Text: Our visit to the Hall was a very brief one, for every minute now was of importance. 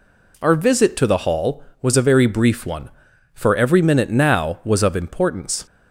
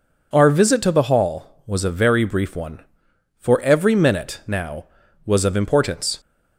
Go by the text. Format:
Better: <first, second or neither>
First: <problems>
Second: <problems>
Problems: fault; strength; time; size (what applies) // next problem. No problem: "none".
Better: neither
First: none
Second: none